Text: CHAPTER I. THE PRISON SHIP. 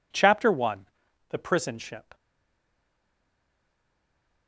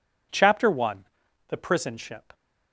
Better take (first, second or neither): second